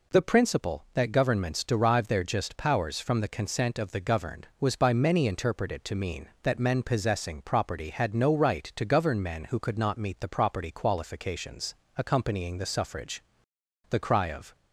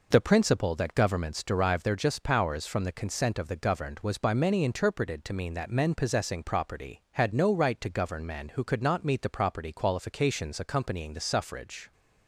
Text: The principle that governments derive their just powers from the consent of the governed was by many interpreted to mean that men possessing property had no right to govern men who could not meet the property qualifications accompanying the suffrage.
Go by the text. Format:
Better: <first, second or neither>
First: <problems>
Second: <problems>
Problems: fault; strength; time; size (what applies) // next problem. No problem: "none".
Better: second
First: pauses between "qualifications" and "accompanying"; slight; at 11.7 s; 0.20 s long // goes on to say "The cry of"; noticeable; from 13.9 s on; 0.64 s long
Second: none